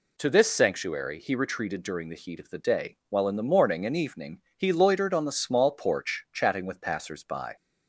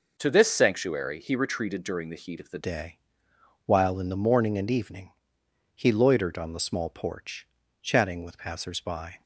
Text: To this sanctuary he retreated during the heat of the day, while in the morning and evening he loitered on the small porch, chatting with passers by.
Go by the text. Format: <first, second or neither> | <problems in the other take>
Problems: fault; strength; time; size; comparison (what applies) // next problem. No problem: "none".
first | changes voice at "day"; from 2.6 s on; 6.6 s long // pauses between "evening" and "he"; noticeable; at 5.1 s; 0.62 s long